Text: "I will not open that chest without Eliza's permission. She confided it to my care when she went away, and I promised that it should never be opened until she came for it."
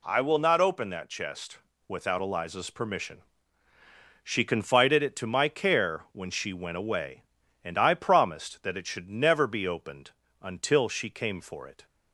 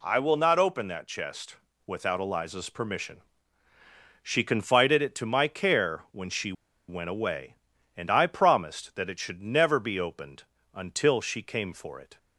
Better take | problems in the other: first | pauses between "chest" and "without"; slight; at 1.5 s; 0.28 s long; slight in the first // pauses between "she" and "went"; slight; at 6.5 s; 0.36 s long // pauses between "opened" and "until"; slight; at 10.4 s; 0.32 s long; slight in the first

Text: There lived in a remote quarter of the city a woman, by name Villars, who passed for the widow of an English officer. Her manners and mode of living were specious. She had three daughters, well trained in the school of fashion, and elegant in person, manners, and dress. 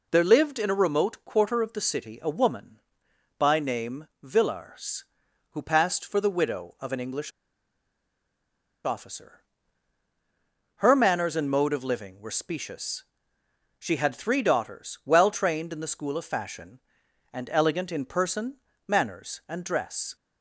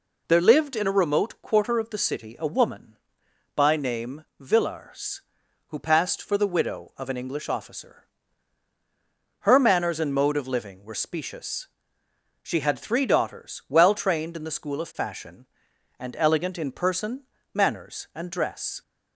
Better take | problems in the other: second | pauses between "English" and "officer"; strong; at 7.2 s; 1.5 s long

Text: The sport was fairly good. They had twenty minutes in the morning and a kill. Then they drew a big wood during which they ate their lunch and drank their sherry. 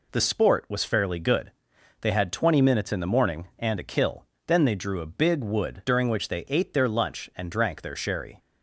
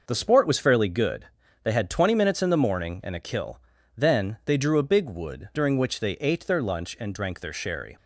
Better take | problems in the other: neither | none

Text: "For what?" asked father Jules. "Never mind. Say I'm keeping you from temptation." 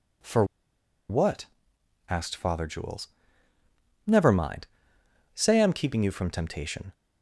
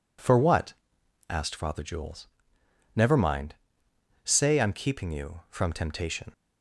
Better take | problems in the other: second | pauses between "For" and "what"; noticeable; at 0.4 s; 0.65 s long

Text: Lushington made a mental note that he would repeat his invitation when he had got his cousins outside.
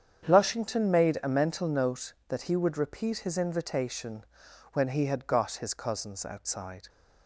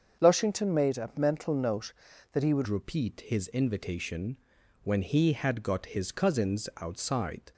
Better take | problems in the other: first | starts louder than the rest; until 1.2 s; 7 dB; strong in the first // changes voice at "repeat"; from 2.6 s on; 4.9 s long // pauses between "invitation" and "when"; noticeable; at 4.3 s; 0.46 s long; noticeable in the first

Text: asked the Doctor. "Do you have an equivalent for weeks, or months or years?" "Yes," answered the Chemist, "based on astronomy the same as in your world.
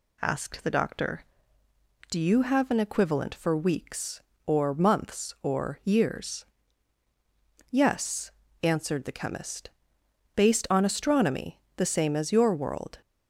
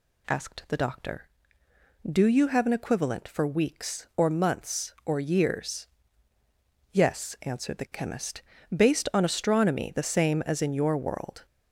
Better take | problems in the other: second | pauses between "astronomy" and "the"; slight; at 11.6 s; 0.16 s long // skips "in"; at 12.3 s

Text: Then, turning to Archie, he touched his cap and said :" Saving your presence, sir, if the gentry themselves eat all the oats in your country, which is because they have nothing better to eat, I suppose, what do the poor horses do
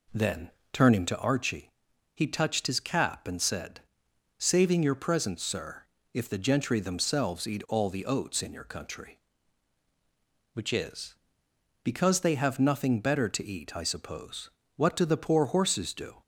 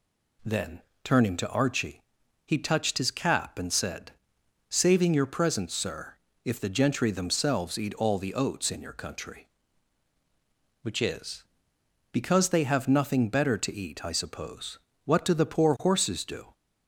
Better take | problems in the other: second | starts louder than the rest; until 1.3 s; 4 dB

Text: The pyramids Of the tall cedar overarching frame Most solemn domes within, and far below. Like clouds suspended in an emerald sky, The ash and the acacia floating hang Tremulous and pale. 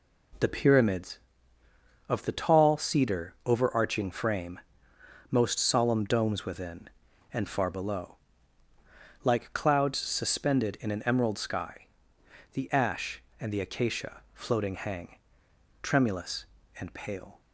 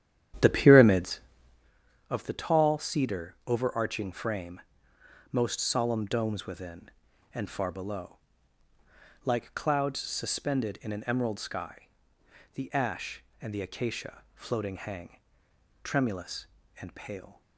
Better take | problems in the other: first | starts louder than the rest; strong; until 1.7 s; 10.5 dB // pauses between "frame" and "Most"; noticeable; at 4.6 s; 0.70 s long; noticeable in the first // pauses between "hang" and "Tremulous"; noticeable; at 15.1 s; 0.64 s long; noticeable in the first

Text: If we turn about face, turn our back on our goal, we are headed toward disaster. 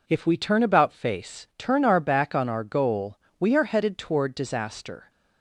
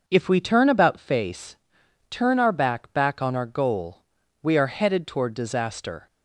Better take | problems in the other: first | says "back" twice; at 2.9 s

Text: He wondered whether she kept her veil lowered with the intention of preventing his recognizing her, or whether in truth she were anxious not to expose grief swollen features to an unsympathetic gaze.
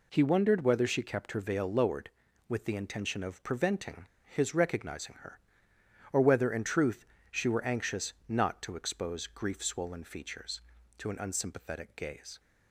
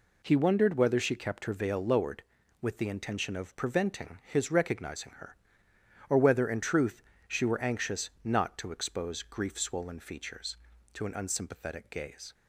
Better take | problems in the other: second | pauses between "preventing" and "his"; slight; at 4.0 s; 0.18 s long // pauses between "truth" and "she"; slight; at 7.0 s; 0.24 s long; slight in the second

